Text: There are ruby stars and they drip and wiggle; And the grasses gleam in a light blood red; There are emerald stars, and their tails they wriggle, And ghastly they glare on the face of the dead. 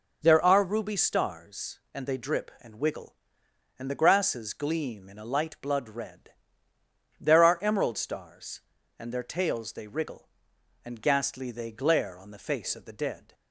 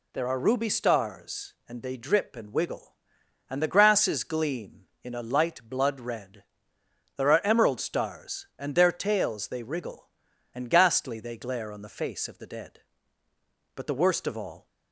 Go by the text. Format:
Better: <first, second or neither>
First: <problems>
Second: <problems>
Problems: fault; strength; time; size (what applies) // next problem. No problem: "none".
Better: first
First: none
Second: goes on to say "But the worst of all"; noticeable; from 13.7 s on; 0.90 s long